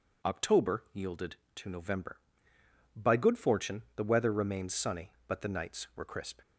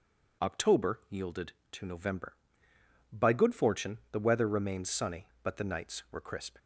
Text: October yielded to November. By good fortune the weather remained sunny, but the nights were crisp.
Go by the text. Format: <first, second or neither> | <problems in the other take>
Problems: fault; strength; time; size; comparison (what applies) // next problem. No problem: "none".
neither | none